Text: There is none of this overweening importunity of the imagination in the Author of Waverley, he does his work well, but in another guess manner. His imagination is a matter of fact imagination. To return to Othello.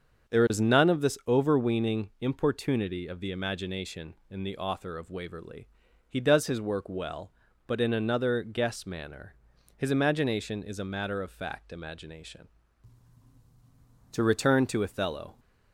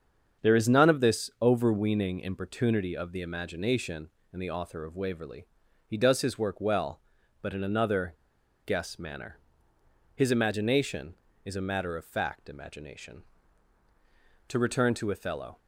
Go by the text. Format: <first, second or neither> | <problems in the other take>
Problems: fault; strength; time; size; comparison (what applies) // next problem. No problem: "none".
first | starts louder than the rest; strong; until 1.5 s; 7.5 dB; also in the first // pauses between "another" and "guess"; noticeable; at 8.1 s; 0.51 s long